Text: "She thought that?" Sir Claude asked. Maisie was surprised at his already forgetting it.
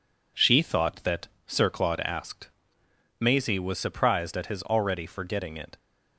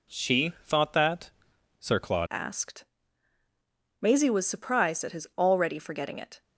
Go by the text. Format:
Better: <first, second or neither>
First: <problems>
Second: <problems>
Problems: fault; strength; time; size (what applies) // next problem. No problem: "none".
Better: first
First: none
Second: changes voice at "asked"; from 2.3 s on; 4.1 s long